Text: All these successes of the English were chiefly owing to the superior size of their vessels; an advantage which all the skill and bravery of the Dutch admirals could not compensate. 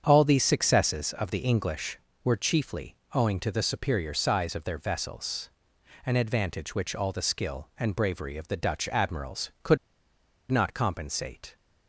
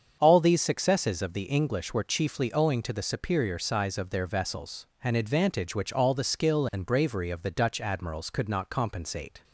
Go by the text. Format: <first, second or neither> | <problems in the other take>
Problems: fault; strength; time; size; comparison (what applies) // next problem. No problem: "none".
second | starts louder than the rest; strong; until 1.0 s; 7.5 dB; strong in the second // pauses between "chiefly" and "owing"; slight; at 2.9 s; 0.20 s long // pauses between "could" and "not"; noticeable; at 9.7 s; 0.74 s long